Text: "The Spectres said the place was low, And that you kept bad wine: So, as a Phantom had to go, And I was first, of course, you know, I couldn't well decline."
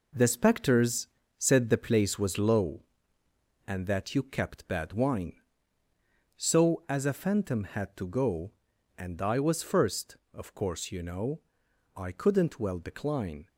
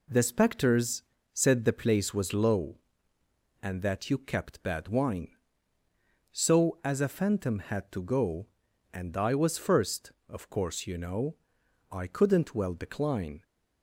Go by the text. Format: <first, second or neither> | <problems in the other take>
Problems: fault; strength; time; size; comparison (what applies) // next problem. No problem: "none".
second | gets quieter; strong; throughout; 7 dB // pauses between "Spectres" and "said"; slight; at 1.0 s; 0.32 s long; slight in the second